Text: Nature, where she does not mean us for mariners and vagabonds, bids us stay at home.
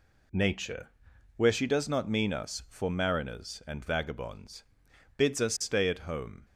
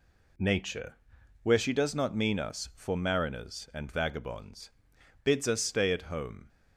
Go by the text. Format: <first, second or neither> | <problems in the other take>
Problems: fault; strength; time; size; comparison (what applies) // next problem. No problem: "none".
neither | none